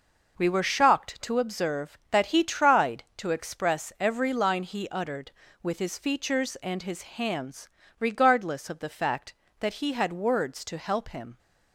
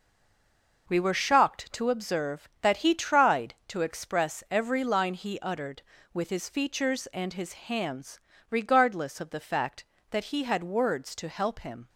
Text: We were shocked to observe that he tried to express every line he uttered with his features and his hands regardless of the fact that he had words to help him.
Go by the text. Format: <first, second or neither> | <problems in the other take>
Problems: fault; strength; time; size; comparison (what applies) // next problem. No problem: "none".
first | stays silent before the first word; slight; until 0.8 s; 0.8 s long // pauses between "hands" and "regardless"; slight; at 8.1 s; 0.32 s long; slight in the first